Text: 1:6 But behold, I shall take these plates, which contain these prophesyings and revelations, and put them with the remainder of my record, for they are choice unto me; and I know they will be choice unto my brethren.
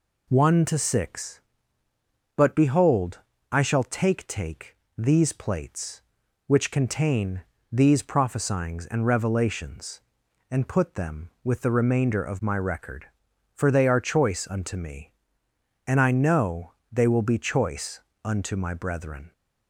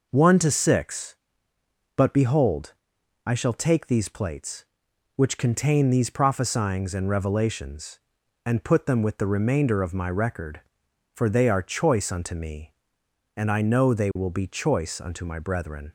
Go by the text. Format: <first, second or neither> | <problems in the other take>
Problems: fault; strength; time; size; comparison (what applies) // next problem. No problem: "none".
second | says "take" twice; at 4.2 s // pauses between "contain" and "these"; slight; at 7.4 s; 0.28 s long // pauses between "know" and "they"; slight; at 16.7 s; 0.18 s long // pauses between "choice" and "unto"; slight; at 17.9 s; 0.24 s long